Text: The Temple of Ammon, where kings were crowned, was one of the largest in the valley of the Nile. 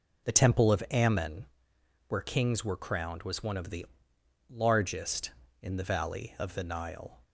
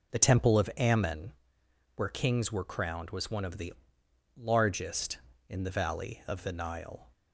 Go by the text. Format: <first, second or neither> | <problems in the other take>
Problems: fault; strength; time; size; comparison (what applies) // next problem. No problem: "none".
neither | pauses between "the" and "largest"; noticeable; the same in both